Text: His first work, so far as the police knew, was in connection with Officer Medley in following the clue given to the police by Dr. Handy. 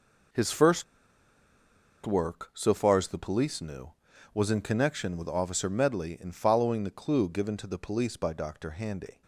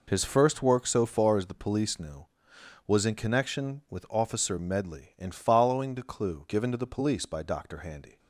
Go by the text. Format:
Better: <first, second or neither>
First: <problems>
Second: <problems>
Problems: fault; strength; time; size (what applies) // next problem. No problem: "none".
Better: second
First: pauses between "first" and "work"; at 0.8 s; 1.2 s long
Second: none